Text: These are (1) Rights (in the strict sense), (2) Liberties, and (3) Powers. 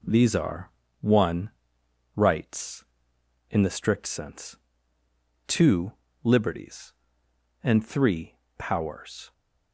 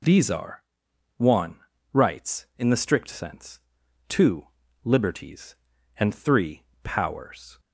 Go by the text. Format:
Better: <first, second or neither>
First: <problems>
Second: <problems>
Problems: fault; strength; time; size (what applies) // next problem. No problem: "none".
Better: neither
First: none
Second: none